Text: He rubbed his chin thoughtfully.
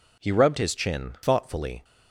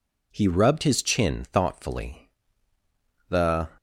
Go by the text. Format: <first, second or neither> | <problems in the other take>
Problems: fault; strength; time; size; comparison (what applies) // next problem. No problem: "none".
first | goes on to say "The"; slight; from 3.2 s on; 0.44 s long